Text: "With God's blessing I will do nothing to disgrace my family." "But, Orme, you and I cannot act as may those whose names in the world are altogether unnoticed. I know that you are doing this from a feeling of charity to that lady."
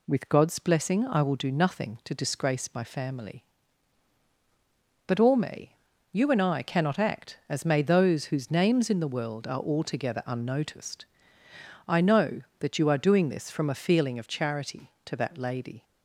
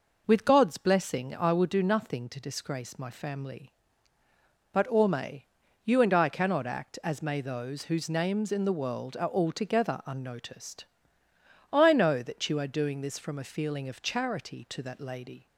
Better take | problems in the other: neither | none

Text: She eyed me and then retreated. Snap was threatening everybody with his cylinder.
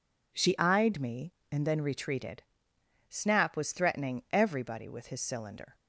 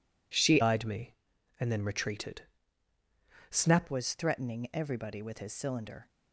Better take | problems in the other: first | changes voice from "eyed" to "Snap"; from 0.6 to 3.8 s; 3.2 s long

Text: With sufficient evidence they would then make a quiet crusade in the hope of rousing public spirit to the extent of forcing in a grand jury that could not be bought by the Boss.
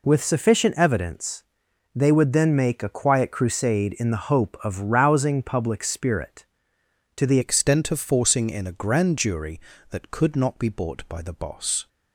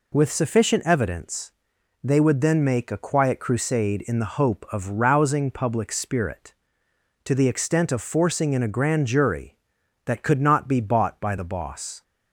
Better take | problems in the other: second | pauses between "evidence" and "they"; noticeable; at 1.4 s; 0.54 s long; noticeable in the second // changes voice at "extent"; from 7.4 s on; 4.4 s long

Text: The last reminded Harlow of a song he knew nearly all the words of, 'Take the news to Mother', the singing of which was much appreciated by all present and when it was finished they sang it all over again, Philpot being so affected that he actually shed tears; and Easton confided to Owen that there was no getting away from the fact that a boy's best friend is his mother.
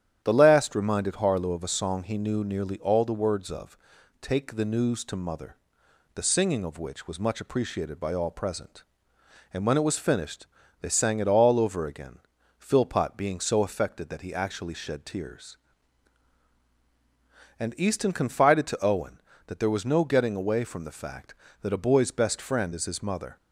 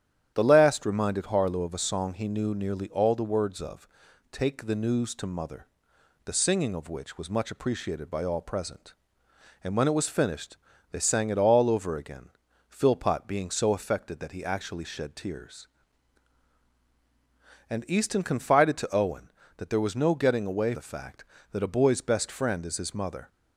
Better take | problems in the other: first | starts louder than the rest; strong; until 1.3 s; 9.5 dB; strong in the first // pauses between "finished" and "they"; slight; at 10.5 s; 0.32 s long; slight in the first // skips "from"; at 20.7 s

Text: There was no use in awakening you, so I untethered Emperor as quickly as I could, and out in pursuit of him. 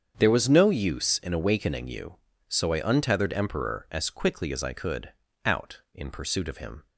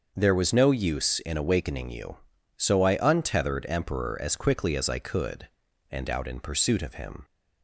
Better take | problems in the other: second | starts louder than the rest; strong; until 1.1 s; 7.5 dB; also in the second // skips "and"; at 5.2 s

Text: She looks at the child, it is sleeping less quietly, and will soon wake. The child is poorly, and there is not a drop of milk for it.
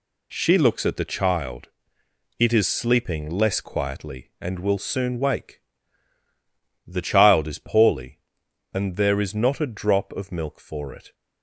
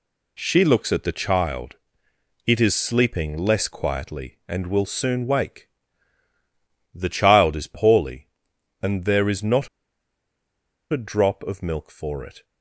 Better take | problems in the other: first | pauses between "not" and "a"; at 9.6 s; 1.2 s long

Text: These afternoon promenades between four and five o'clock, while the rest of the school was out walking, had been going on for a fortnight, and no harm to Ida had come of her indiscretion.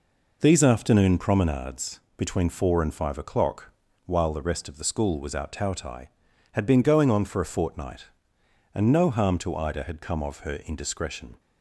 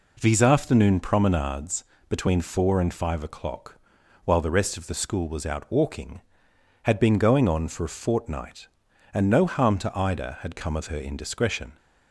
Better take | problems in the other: second | pauses between "promenades" and "between"; slight; at 2.0 s; 0.16 s long; slight in the second // says "tautai" for "walking"; at 5.5 s

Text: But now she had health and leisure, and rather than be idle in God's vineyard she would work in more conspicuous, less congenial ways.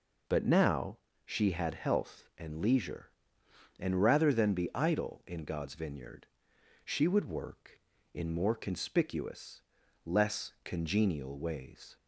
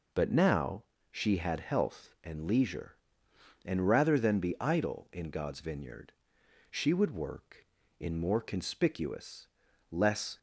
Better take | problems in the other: first | pauses between "now" and "she"; slight; at 0.8 s; 0.26 s long; slight in the first // pauses between "vineyard" and "she"; noticeable; at 6.1 s; 0.58 s long; noticeable in the first // stops before "congenial ways"; at 10.3 s

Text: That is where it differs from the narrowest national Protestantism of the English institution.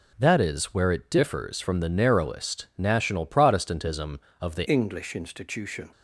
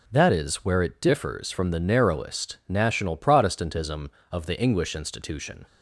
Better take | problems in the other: second | changes voice at "English"; from 4.6 s on; 1.3 s long

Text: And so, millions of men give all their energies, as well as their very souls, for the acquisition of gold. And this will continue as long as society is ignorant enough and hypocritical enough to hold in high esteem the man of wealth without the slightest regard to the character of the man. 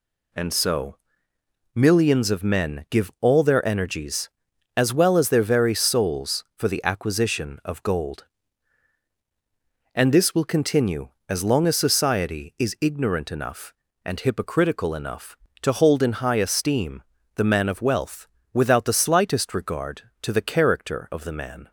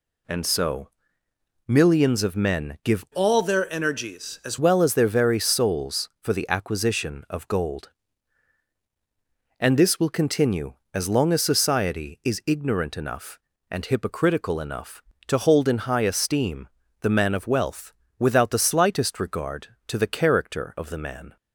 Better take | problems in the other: first | changes voice from "all" to "as"; from 3.1 to 4.5 s; 1.4 s long // pauses between "esteem" and "the"; slight; at 16.6 s; 0.32 s long; slight in the first // pauses between "wealth" and "without"; slight; at 17.9 s; 0.26 s long; slight in the first

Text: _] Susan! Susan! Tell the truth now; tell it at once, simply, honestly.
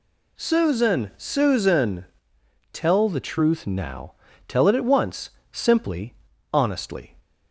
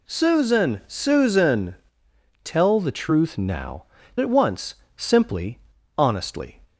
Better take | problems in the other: first | skips "tell it"; at 4.0 s

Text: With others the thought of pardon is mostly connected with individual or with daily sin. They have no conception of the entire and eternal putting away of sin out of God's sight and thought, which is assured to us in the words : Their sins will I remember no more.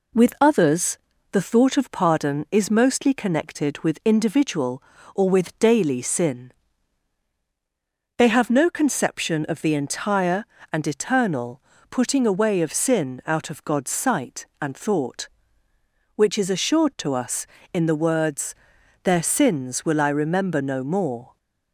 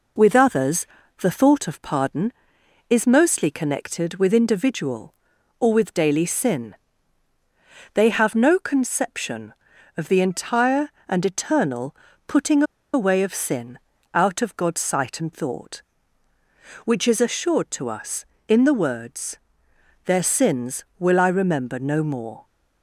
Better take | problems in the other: first | pauses between "others" and "the"; slight; at 0.8 s; 0.32 s long; slight in the first // pauses between "eternal" and "putting"; slight; at 11.9 s; 0.32 s long; slight in the first // pauses between "putting" and "away"; slight; at 12.6 s; 0.30 s long // pauses between "sin" and "out"; slight; at 13.7 s; 0.34 s long

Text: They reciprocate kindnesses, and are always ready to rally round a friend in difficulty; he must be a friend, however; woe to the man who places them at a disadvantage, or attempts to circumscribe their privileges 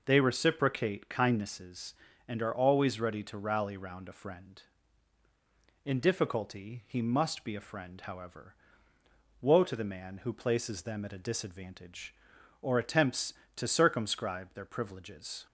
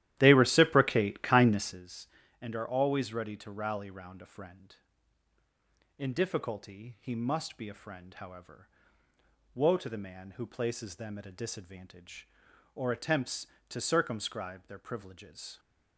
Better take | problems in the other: first | starts louder than the rest; strong; until 1.9 s; 13.5 dB

